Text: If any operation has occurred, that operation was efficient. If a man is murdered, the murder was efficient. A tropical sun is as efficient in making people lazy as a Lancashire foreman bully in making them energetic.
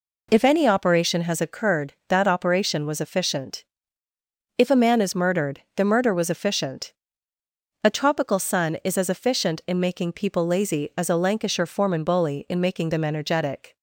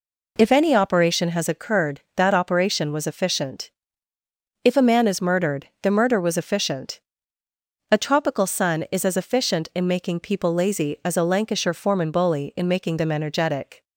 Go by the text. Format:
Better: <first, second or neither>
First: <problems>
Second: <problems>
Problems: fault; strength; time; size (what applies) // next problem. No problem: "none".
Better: neither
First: none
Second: none